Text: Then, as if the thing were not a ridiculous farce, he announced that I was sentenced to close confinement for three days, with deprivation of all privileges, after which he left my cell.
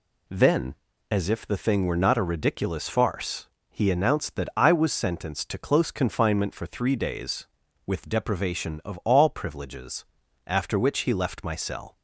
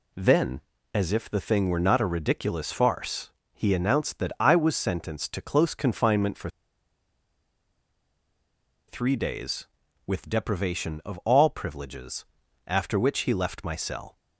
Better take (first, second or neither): first